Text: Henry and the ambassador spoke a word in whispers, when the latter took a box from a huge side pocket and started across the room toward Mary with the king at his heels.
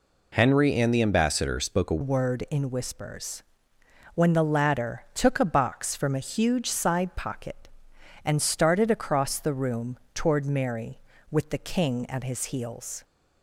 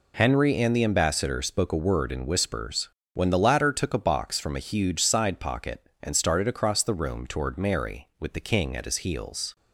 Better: second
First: changes voice at "word"; from 2.0 s on; 11.0 s long // pauses between "room" and "toward"; slight; at 9.9 s; 0.16 s long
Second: none

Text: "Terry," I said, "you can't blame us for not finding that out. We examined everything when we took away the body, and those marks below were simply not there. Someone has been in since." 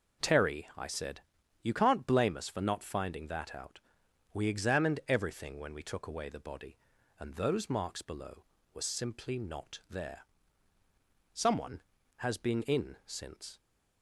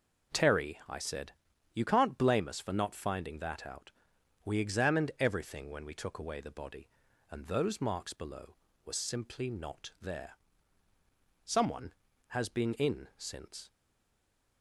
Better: first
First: none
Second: stays silent after the last word; slight; from 13.7 s on; 0.9 s long

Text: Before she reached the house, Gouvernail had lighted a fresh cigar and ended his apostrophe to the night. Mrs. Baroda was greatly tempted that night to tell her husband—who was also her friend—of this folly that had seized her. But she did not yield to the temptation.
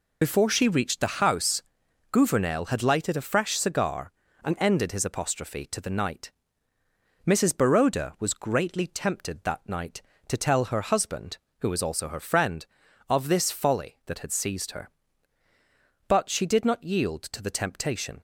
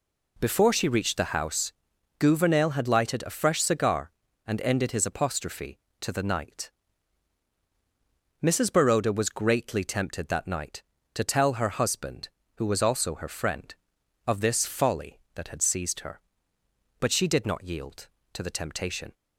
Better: second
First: loses the start of "Before"; at 0.2 s; 50 ms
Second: none

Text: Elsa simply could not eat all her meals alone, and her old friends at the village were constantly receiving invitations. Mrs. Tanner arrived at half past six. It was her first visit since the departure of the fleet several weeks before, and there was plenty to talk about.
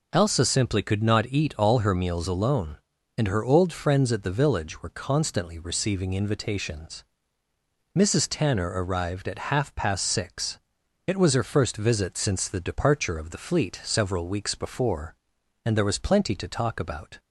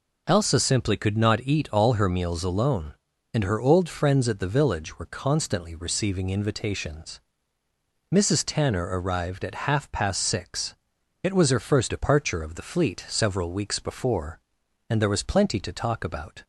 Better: first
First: none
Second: skips "visit since the"; at 11.8 s

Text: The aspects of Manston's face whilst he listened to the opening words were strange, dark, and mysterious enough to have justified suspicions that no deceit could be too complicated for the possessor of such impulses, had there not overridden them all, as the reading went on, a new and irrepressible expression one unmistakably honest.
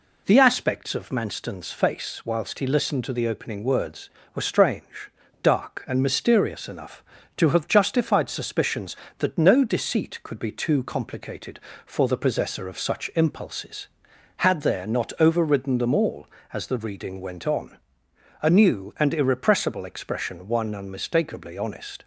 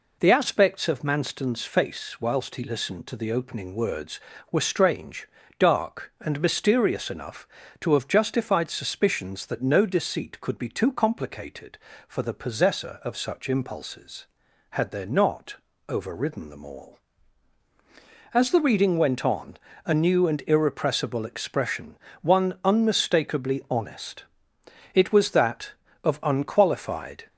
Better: first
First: none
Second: pauses between "not" and "overridden"; slight; at 15.5 s; 0.32 s long // pauses between "expression" and "one"; slight; at 21.9 s; 0.28 s long // goes on to say "It was that of unqualified"; strong; from 24.9 s on; 2.3 s long

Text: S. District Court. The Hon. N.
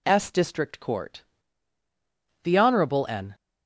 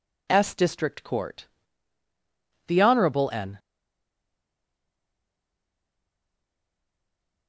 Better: first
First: none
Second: stays silent after the last word; strong; from 3.5 s on; 3.9 s long

